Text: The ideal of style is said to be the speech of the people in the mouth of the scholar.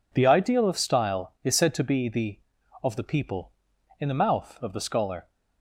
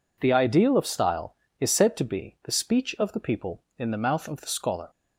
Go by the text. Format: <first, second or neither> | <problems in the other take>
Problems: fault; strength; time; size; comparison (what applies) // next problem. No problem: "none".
second | skips "speech"; at 2.6 s